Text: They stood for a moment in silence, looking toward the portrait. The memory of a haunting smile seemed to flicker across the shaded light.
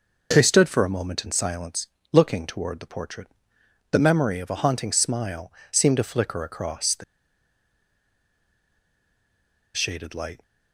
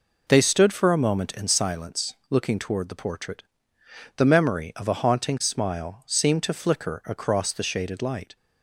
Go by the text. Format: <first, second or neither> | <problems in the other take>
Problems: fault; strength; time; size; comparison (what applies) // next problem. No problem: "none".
second | pauses between "smile" and "seemed"; slight; at 5.5 s; 0.20 s long // pauses between "the" and "shaded"; strong; at 7.0 s; 2.7 s long